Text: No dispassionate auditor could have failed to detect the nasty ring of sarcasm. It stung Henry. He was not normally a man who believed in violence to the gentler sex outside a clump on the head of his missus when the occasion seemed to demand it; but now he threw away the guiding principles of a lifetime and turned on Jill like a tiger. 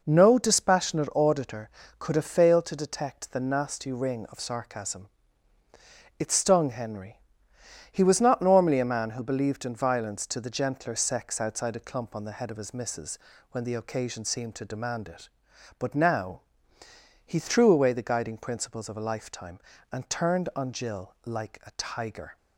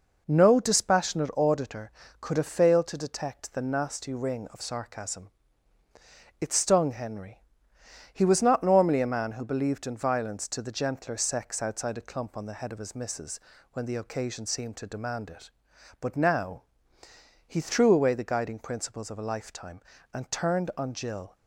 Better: first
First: pauses between "missus" and "when"; slight; at 13.1 s; 0.36 s long // pauses between "now" and "he"; noticeable; at 16.4 s; 0.84 s long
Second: pauses between "missus" and "when"; slight; at 13.3 s; 0.36 s long // pauses between "now" and "he"; noticeable; at 16.6 s; 0.84 s long // stops before "like a tiger"; at 21.3 s

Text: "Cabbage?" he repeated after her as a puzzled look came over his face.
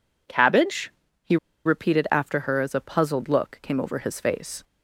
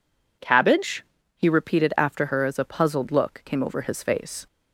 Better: second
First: pauses between "he" and "repeated"; slight; at 1.3 s; 0.28 s long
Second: none

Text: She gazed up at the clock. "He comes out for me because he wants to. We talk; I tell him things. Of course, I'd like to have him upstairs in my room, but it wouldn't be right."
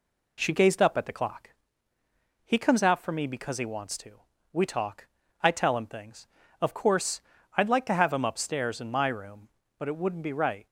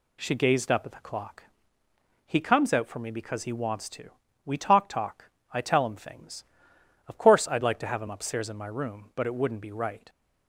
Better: first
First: none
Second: says "talk" twice; at 4.8 s

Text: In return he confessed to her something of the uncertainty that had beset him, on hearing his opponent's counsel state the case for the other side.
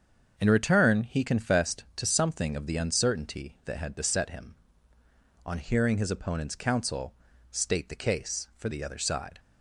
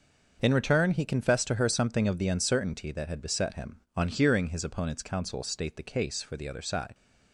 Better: second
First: starts louder than the rest; until 1.3 s; 7 dB // skips "her"; at 2.0 s // pauses between "counsel" and "state"; slight; at 7.1 s; 0.36 s long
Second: starts louder than the rest; until 1.4 s; 6.5 dB

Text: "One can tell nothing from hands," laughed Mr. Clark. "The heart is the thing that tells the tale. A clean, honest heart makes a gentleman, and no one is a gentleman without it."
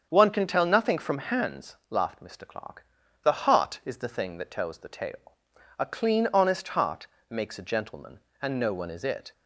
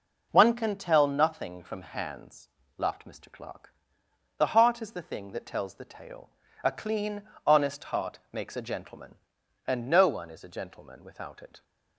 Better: second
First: starts louder than the rest; strong; until 1.1 s; 7.5 dB // pauses between "heart" and "makes"; slight; at 7.0 s; 0.20 s long // skips "a gentleman without"; at 9.0 s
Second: none

